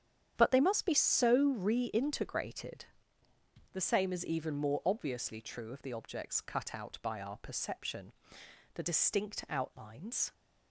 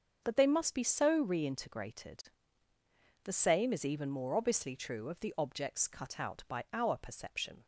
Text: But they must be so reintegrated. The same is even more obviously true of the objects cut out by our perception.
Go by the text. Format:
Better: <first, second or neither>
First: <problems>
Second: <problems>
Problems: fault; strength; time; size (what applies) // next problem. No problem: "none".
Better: second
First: starts louder than the rest; strong; until 1.3 s; 9 dB // goes on to say "The distinct outlines"; from 8.7 s on; 1.5 s long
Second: starts louder than the rest; until 1.2 s; 6.5 dB